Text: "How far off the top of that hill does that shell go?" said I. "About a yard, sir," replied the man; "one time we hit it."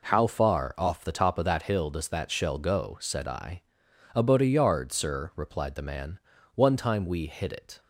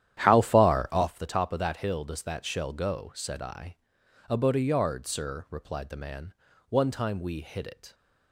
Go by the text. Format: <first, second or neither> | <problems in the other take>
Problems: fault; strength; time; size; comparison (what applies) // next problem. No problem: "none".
first | starts louder than the rest; strong; until 1.1 s; 11 dB